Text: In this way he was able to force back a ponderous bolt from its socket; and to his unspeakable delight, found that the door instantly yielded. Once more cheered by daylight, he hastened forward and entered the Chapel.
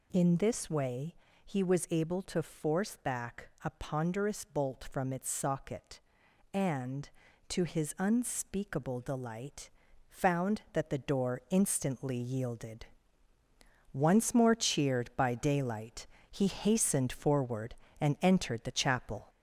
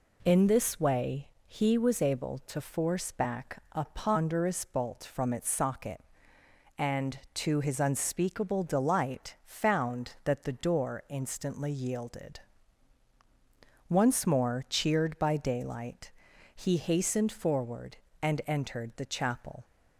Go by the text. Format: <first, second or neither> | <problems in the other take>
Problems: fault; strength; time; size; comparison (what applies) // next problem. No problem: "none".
second | gets louder; slight; throughout; 3 dB // pauses between "way" and "he"; slight; at 1.1 s; 0.30 s long; slight in the second